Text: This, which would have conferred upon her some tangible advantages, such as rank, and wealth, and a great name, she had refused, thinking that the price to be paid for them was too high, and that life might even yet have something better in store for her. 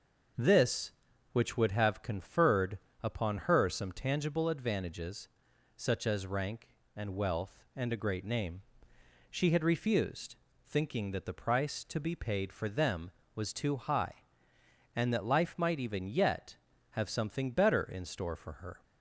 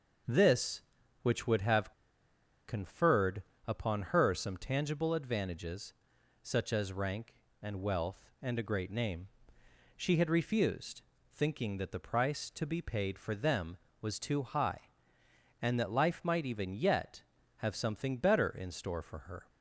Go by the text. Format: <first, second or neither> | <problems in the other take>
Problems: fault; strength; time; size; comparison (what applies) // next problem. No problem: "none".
first | pauses between "have" and "conferred"; noticeable; at 1.9 s; 0.75 s long // pauses between "conferred" and "upon"; slight; at 3.4 s; 0.24 s long; slight in the first